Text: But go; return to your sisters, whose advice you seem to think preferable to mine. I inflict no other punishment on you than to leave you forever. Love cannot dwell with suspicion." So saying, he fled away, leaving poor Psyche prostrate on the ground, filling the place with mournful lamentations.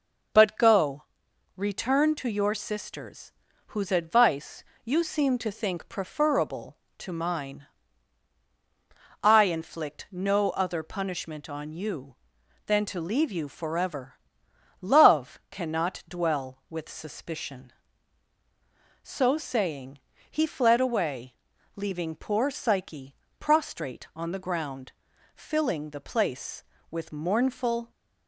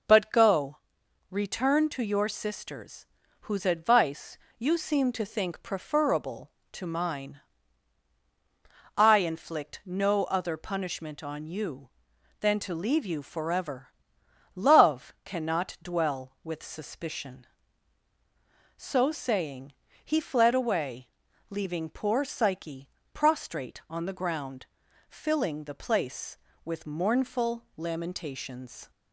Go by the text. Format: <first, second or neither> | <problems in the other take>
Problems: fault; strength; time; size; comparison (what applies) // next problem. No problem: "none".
second | pauses between "advice" and "you"; slight; at 4.6 s; 0.20 s long; slight in the second // pauses between "Psyche" and "prostrate"; slight; at 23.1 s; 0.24 s long; slight in the second // stops before "lamentations"; at 27.9 s